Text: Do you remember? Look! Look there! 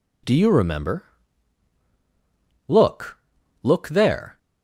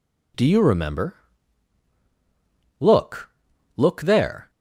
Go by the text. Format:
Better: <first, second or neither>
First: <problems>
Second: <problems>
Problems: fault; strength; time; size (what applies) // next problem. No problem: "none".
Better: neither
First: none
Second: none